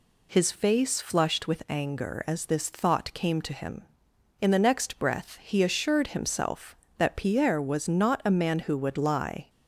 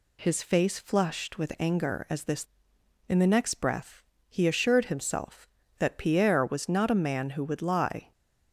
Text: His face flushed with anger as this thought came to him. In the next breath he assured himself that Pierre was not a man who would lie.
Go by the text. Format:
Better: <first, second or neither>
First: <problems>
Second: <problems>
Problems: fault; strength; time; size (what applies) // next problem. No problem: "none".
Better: first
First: none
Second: skips "thought came to him"; at 2.7 s // pauses between "breath" and "he"; slight; at 4.0 s; 0.26 s long